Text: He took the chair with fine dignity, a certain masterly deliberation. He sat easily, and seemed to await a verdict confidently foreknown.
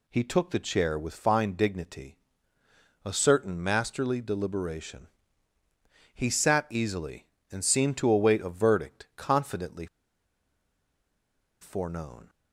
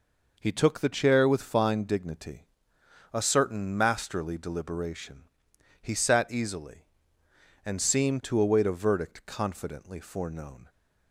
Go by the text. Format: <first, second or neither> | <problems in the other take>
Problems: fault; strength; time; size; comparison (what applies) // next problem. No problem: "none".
second | pauses between "confidently" and "foreknown"; strong; at 9.8 s; 1.7 s long